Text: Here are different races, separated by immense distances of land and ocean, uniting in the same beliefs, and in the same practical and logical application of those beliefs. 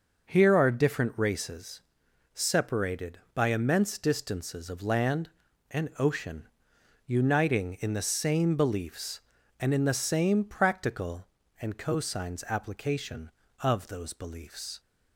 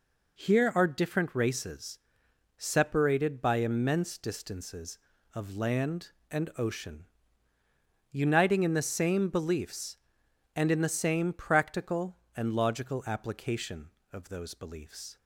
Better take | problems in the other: second | says "cosines" for "logical"; at 11.7 s

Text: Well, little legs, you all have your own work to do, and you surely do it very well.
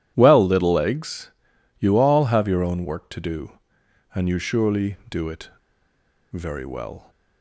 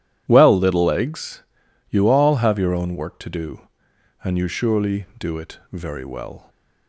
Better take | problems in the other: second | pauses between "it" and "very"; noticeable; at 5.4 s; 0.82 s long

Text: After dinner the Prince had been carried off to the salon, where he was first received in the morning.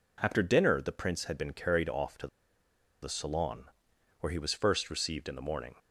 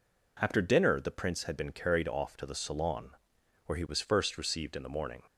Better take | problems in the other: second | pauses between "to" and "the"; noticeable; at 2.2 s; 0.75 s long

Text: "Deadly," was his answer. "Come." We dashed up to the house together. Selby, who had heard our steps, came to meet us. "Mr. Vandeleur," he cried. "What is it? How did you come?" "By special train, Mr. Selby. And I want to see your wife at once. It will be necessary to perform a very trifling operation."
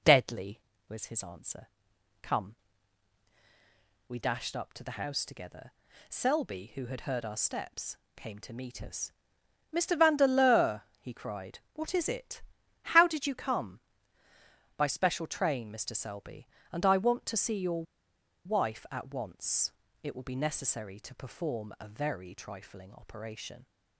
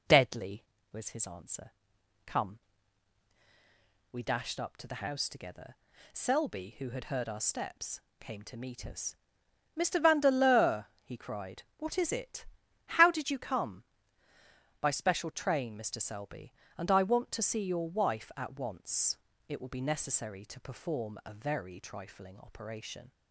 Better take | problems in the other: second | pauses between "your" and "wife"; noticeable; at 17.8 s; 0.61 s long

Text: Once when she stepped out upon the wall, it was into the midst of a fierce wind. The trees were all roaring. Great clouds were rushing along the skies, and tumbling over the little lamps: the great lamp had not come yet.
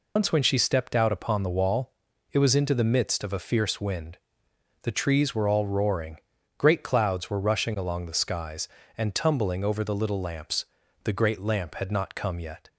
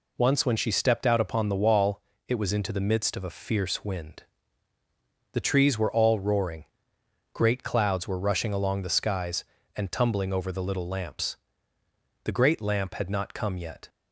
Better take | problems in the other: second | loses the start of "Once"; at 0.1 s; 110 ms

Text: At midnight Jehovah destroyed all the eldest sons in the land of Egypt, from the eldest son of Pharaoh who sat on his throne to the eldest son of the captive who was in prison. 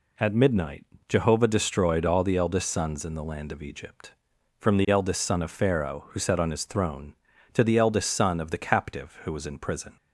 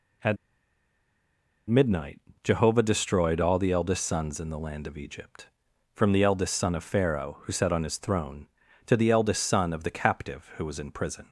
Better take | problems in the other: first | pauses between "At" and "midnight"; strong; at 0.3 s; 1.3 s long // pauses between "midnight" and "Jehovah"; slight; at 2.2 s; 0.22 s long; slight in the first

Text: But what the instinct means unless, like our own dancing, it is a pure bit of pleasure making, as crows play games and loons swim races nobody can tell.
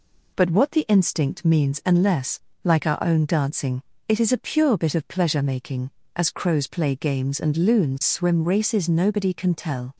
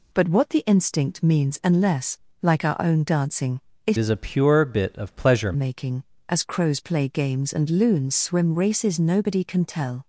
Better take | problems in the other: first | changes voice from "is" to "pleasure"; from 3.9 to 5.5 s; 1.6 s long

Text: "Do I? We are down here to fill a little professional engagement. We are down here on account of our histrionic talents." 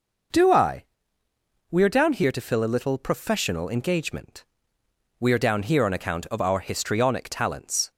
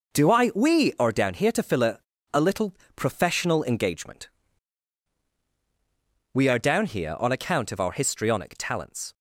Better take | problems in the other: first | says "a" twice; at 2.3 s // pauses between "little" and "professional"; slight; at 2.7 s; 0.20 s long

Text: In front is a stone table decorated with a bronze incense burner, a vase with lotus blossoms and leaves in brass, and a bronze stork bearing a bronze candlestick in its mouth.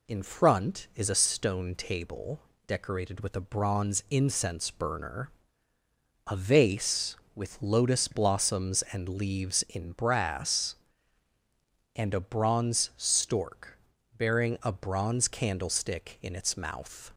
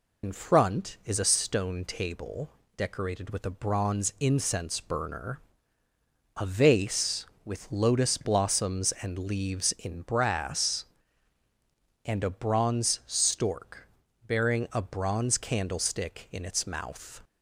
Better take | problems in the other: first | loses the start of "In"; at 0.2 s; 60 ms // pauses between "table" and "decorated"; slight; at 2.4 s; 0.26 s long; slight in the first // pauses between "stork" and "bearing"; at 13.8 s; 0.40 s long; also in the first

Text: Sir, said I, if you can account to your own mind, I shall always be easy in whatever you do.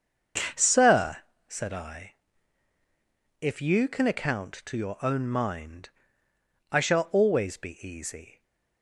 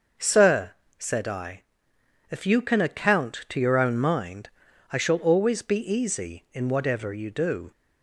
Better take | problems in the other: second | starts louder than the rest; until 1.8 s; 6.5 dB; also in the second // stops before "in whatever you do"; at 8.4 s

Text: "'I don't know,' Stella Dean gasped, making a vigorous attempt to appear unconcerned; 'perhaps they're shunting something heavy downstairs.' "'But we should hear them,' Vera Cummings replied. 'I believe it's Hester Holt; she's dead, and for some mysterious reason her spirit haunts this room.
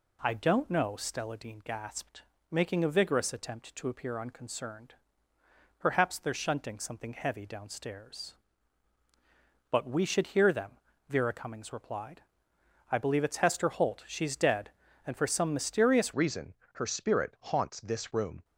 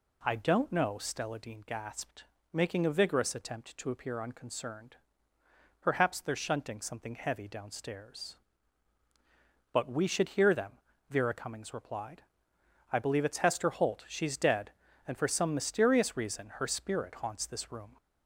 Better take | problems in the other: second | changes voice at "reason"; from 16.1 s on; 2.3 s long // pauses between "reason" and "her"; slight; at 16.5 s; 0.20 s long

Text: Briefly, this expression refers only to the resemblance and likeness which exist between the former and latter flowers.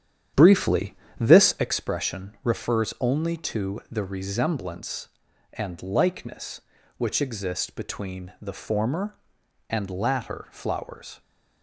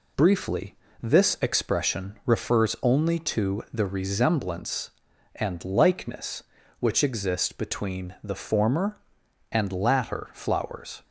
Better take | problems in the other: second | starts louder than the rest; strong; until 1.7 s; 9.5 dB

